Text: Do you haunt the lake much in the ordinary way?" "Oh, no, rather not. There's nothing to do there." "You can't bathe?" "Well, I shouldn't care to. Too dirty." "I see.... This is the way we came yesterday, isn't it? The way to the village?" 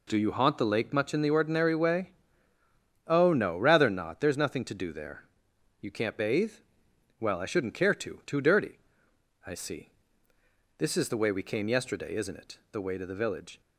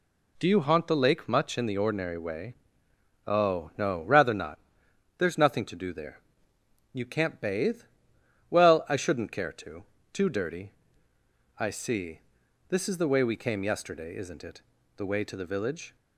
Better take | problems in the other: neither | none

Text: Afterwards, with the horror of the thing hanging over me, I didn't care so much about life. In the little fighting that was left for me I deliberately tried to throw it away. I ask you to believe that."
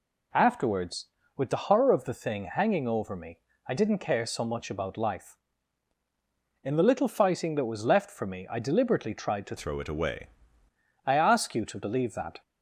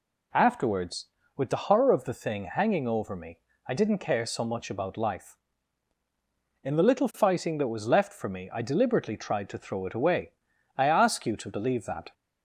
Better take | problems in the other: second | changes voice from "throw" to "away"; from 9.5 to 10.2 s; 0.7 s long

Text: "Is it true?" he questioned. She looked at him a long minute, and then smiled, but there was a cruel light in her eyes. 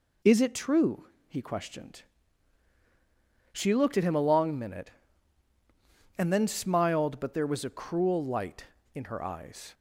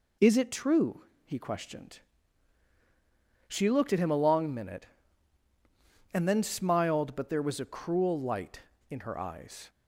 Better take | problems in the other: neither | none

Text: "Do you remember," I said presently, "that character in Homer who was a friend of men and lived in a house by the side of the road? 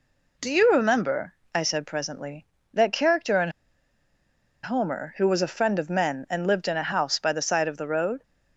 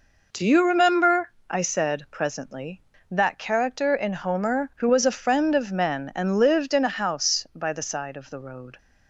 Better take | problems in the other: second | pauses between "in" and "Homer"; at 3.4 s; 1.1 s long

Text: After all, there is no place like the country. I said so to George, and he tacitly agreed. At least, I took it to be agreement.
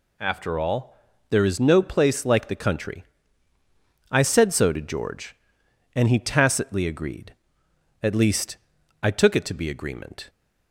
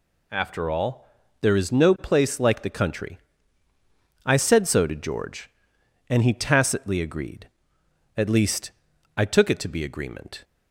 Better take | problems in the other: neither | none

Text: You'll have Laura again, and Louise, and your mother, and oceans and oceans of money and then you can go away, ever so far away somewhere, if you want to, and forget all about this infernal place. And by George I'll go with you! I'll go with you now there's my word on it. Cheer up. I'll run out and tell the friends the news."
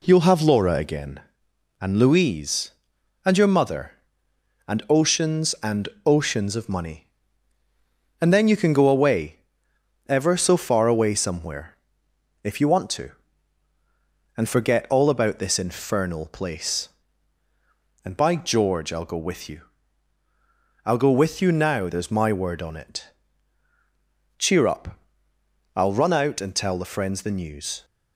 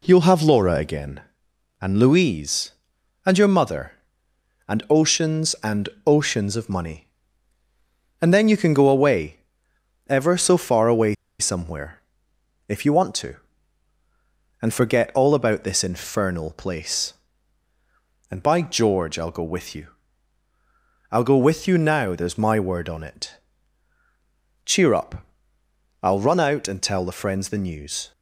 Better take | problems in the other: first | pauses between "and" and "oceans"; slight; at 5.8 s; 0.18 s long; slight in the first // pauses between "away" and "somewhere"; slight; at 11.1 s; 0.26 s long

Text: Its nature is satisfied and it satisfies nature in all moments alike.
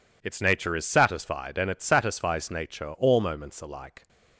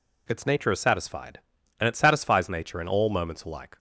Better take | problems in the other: second | skips "in"; at 2.9 s

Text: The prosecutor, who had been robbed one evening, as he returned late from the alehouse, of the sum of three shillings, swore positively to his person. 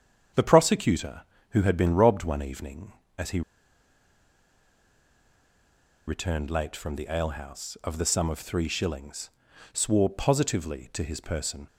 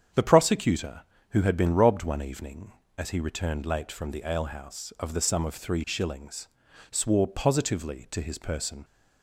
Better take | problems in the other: second | starts louder than the rest; strong; until 1.6 s; 8 dB; strong in the second // pauses between "he" and "returned"; strong; at 3.4 s; 2.6 s long

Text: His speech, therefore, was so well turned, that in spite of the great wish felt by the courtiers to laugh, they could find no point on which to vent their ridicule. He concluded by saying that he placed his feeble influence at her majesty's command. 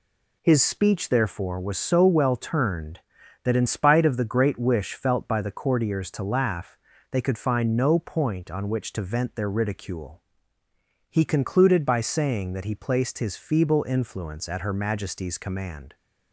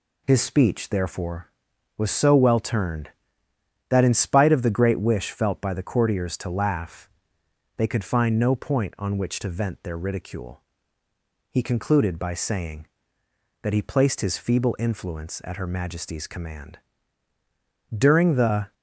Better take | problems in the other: first | goes on to say "During the"; noticeable; from 17.9 s on; 0.78 s long

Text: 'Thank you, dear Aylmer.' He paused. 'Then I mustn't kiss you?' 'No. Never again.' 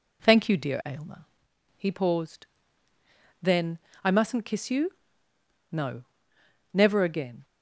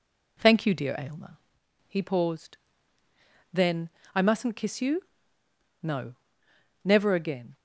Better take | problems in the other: neither | pauses between "Then" and "I"; slight; the same in both

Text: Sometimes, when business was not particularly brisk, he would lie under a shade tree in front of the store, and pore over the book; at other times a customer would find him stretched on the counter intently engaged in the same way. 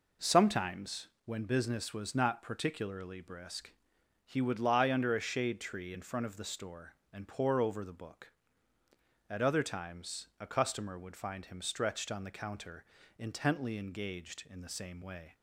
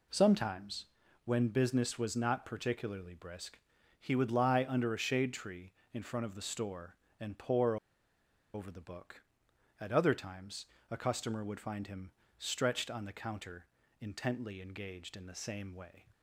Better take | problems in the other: first | pauses between "pore" and "over"; noticeable; at 7.7 s; 0.77 s long // pauses between "times" and "a"; slight; at 10.6 s; 0.24 s long // pauses between "him" and "stretched"; slight; at 12.0 s; 0.28 s long // pauses between "counter" and "intently"; slight; at 13.6 s; 0.34 s long; slight in the first

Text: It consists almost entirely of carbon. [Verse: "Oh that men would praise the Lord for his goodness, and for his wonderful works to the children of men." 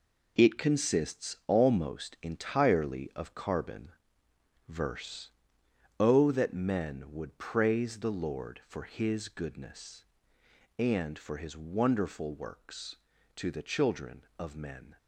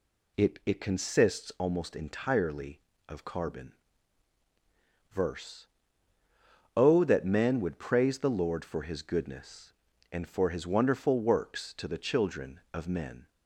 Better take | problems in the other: first | says "It" twice; at 0.6 s

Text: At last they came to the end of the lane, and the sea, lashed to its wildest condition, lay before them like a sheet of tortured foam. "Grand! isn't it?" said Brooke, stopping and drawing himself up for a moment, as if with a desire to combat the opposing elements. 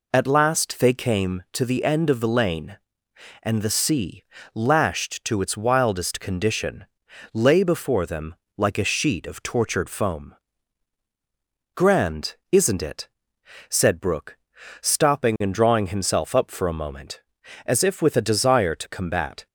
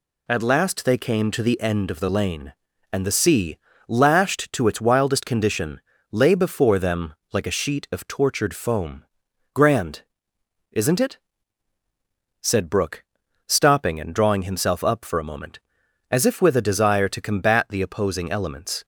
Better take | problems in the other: second | pauses between "them" and "like"; slight; at 8.3 s; 0.22 s long; slight in the second // stops before "the opposing elements"; at 19.4 s

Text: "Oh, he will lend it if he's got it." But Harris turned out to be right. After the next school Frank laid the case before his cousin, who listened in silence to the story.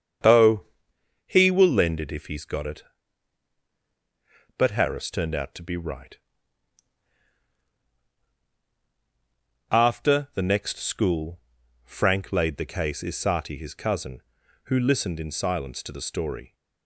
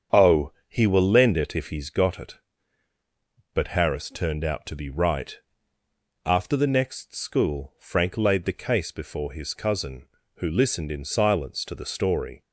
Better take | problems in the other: second | starts louder than the rest; strong; until 1.8 s; 7.5 dB; strong in the second // pauses between "school" and "Frank"; at 11.4 s; 0.42 s long // says "isati" for "before"; at 13.0 s

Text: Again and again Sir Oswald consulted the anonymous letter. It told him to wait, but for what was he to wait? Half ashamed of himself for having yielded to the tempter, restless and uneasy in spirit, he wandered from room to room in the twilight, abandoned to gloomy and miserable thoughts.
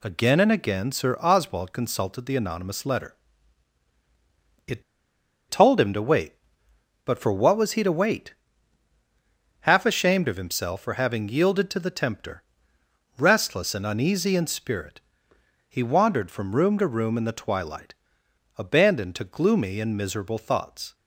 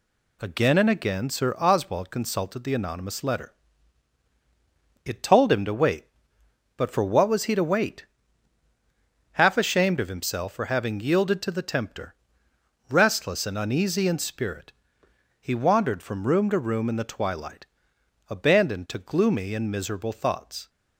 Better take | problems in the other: second | pauses between "It" and "told"; noticeable; at 4.8 s; 0.68 s long

